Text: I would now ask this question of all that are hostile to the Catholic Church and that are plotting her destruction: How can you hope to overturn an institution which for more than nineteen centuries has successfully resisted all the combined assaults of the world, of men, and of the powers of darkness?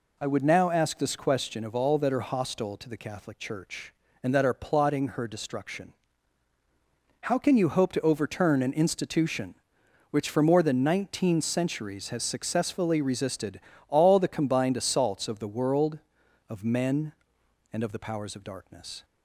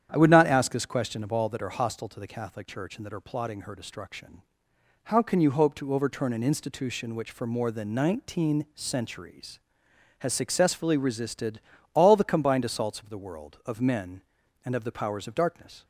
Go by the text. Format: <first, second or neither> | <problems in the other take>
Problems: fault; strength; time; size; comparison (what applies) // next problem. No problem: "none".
first | starts louder than the rest; strong; until 1.1 s; 9.5 dB // says "not" for "now"; at 0.3 s // pauses between "resisted" and "all"; slight; at 11.6 s; 0.32 s long; slight in the first